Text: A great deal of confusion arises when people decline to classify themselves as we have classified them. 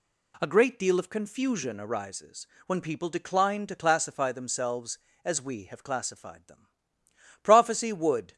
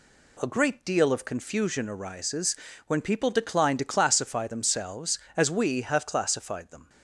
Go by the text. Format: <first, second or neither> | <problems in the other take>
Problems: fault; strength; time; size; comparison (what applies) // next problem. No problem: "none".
second | pauses between "arises" and "when"; slight; at 2.4 s; 0.22 s long; slight in the second // goes on to say "Prophecy would"; noticeable; from 7.4 s on; 0.92 s long